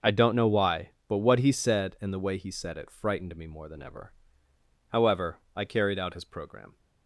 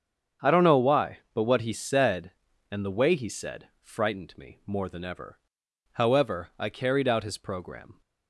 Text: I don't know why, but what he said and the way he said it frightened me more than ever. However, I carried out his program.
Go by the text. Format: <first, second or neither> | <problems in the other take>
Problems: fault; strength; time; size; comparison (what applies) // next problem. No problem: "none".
first | starts louder than the rest; strong; until 1.5 s; 7.5 dB; noticeable in the first // skips "it"; at 3.7 s